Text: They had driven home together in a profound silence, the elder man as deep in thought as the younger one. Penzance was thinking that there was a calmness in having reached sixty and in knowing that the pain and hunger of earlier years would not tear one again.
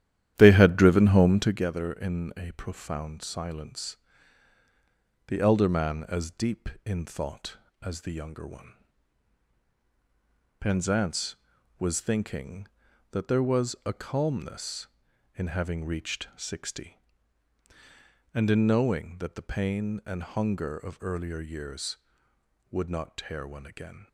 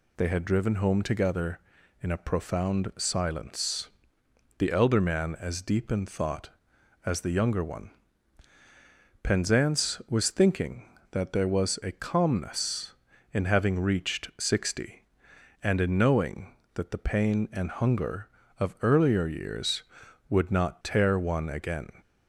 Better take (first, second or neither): second